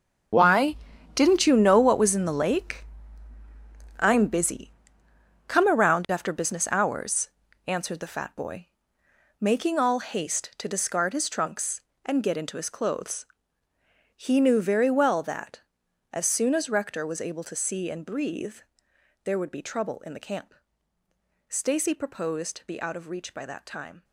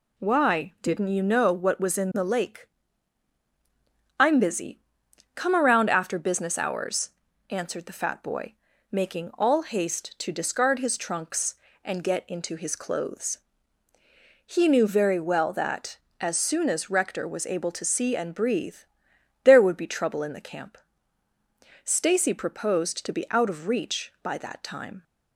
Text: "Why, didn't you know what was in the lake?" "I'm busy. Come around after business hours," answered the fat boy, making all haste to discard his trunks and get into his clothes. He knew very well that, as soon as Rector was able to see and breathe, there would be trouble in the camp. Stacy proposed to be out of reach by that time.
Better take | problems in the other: second | gets quieter; strong; throughout; 13 dB

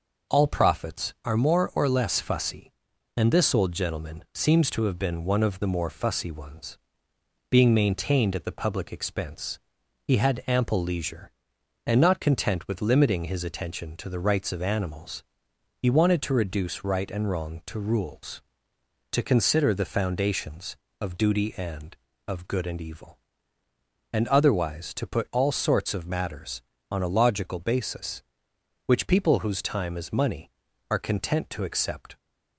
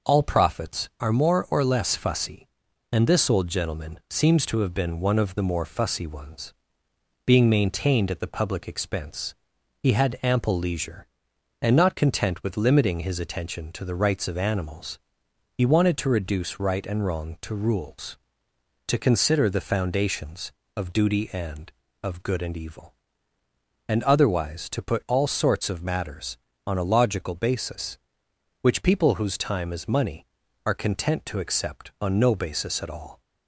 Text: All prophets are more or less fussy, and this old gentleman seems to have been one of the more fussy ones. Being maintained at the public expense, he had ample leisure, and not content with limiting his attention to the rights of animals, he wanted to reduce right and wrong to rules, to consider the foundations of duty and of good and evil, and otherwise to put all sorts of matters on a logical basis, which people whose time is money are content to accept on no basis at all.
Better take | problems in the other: second | stops before "on no basis at all"; at 32.1 s

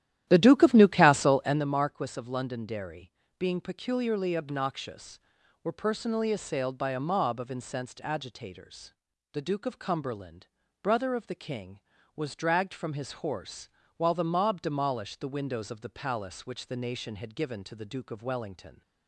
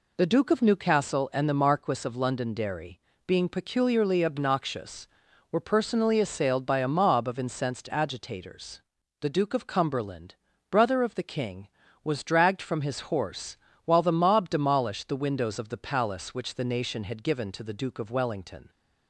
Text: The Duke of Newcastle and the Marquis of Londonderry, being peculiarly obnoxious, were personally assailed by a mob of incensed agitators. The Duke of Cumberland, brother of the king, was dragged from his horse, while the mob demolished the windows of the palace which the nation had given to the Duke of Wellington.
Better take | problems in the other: second | starts louder than the rest; strong; until 1.7 s; 12.5 dB

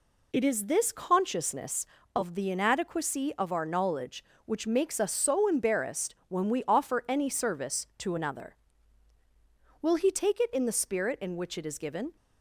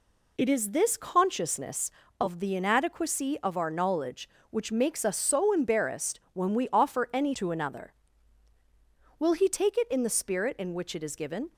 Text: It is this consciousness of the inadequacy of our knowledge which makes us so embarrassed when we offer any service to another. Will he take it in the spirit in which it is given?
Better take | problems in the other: first | skips "service"; at 7.3 s

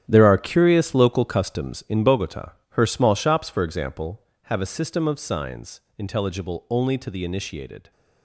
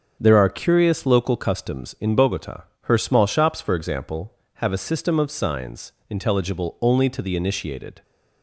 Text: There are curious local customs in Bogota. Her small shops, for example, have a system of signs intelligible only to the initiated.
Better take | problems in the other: second | gets quieter; strong; throughout; 12.5 dB // starts louder than the rest; strong; until 1.0 s; 10.5 dB; also in the second // pauses between "signs" and "intelligible"; slight; at 5.8 s; 0.16 s long; slight in the second

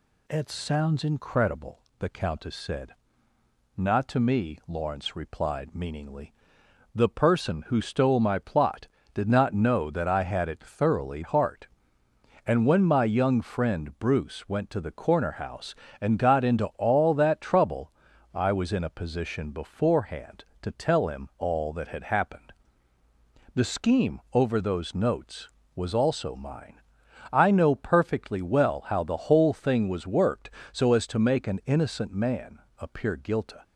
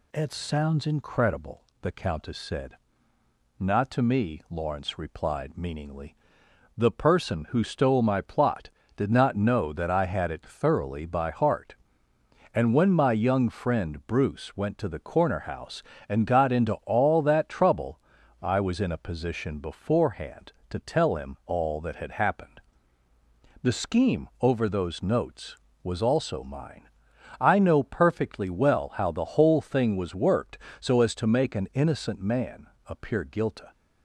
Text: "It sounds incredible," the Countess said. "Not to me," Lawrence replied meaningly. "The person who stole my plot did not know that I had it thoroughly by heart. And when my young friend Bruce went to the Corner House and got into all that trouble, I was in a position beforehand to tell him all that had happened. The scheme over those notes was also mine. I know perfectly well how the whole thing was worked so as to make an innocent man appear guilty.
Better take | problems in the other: second | skips "by"; at 11.2 s // pauses between "man" and "appear"; slight; at 32.5 s; 0.18 s long; slight in the second

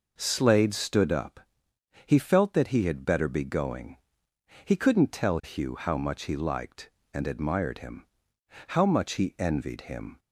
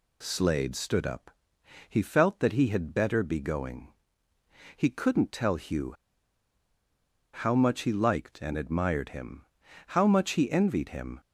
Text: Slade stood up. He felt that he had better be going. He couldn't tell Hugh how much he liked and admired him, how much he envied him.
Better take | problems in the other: first | pauses between "Hugh" and "how"; strong; at 5.9 s; 1.3 s long

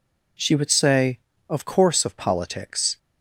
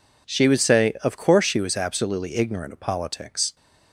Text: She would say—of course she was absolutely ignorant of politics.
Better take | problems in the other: second | skips "she was absolutely ignorant"; at 2.0 s

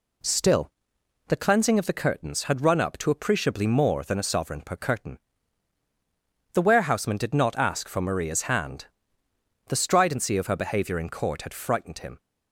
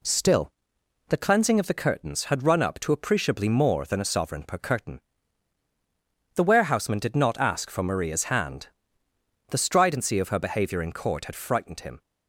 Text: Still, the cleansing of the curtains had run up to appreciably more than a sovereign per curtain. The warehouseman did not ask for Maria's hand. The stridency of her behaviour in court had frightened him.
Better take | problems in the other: neither | none

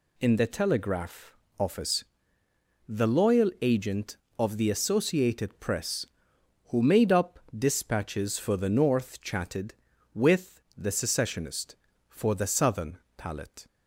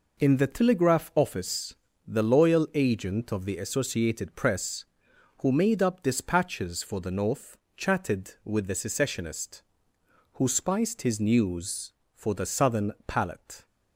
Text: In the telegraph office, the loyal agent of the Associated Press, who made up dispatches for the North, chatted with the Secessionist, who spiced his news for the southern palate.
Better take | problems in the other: second | pauses between "telegraph" and "office"; slight; at 1.3 s; 0.24 s long // pauses between "up" and "dispatches"; slight; at 7.3 s; 0.18 s long // skips "who spiced his news"; at 11.9 s // pauses between "southern" and "palate"; slight; at 12.9 s; 0.22 s long

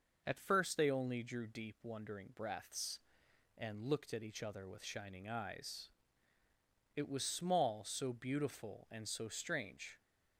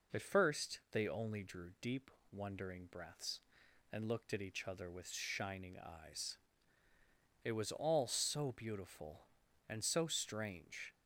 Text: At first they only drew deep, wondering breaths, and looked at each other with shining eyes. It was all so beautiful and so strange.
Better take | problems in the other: second | says "small" for "all"; at 7.2 s

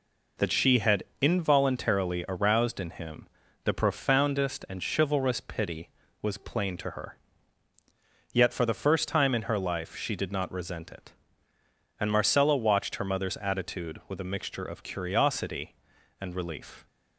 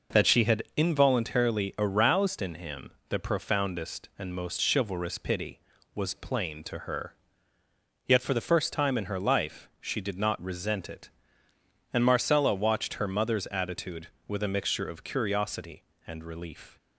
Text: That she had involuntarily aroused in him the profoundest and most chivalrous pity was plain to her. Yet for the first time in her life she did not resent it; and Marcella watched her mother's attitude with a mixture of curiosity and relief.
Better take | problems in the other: second | pauses between "had" and "involuntarily"; slight; at 1.0 s; 0.18 s long // pauses between "him" and "the"; slight; at 3.2 s; 0.36 s long; slight in the second // skips "most"; at 4.8 s

